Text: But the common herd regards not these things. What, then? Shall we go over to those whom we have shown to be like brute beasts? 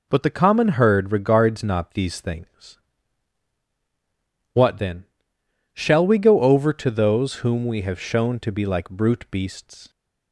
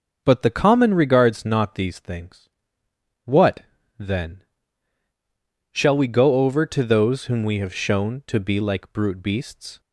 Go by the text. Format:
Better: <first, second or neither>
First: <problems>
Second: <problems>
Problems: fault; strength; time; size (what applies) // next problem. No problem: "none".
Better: first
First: none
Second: starts louder than the rest; until 1.2 s; 6.5 dB // skips "herd"; at 0.9 s